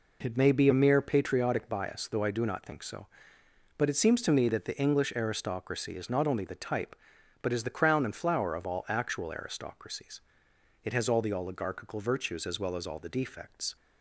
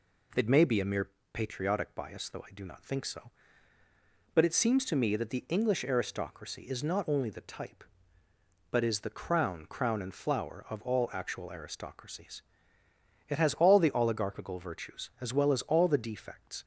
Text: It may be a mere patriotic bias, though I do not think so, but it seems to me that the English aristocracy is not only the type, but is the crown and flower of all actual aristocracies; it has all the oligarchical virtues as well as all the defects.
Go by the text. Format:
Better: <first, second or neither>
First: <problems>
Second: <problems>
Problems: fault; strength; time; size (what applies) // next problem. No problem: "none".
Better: first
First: none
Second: pauses between "mere" and "patriotic"; slight; at 1.0 s; 0.24 s long // says "crown" twice; at 9.6 s